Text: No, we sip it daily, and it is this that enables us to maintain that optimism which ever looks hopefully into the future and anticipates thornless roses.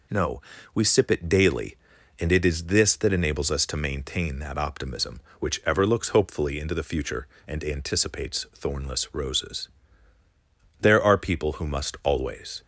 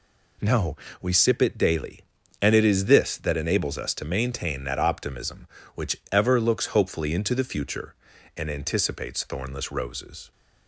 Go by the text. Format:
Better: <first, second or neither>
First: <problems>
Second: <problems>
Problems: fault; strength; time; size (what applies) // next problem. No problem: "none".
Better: second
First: goes on to say "There are people who must always"; strong; from 10.7 s on; 1.8 s long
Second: none